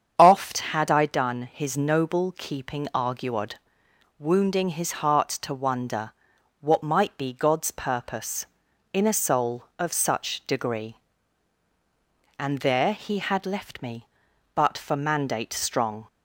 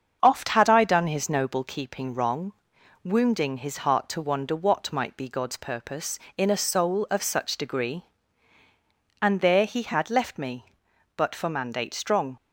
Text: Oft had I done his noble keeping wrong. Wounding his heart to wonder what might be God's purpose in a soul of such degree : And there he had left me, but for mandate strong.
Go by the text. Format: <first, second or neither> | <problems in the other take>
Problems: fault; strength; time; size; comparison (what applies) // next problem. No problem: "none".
second | starts louder than the rest; strong; until 1.1 s; 7.5 dB; also in the second // says "arguod" for "wrong"; at 2.9 s // pauses between "wonder" and "what"; noticeable; at 6.1 s; 0.48 s long